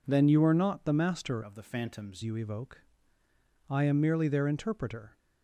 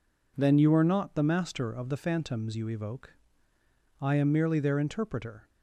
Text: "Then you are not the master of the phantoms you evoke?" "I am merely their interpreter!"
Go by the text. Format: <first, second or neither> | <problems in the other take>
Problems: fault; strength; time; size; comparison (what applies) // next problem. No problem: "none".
second | changes voice from "of" to "phantoms"; from 1.4 to 2.2 s; 0.8 s long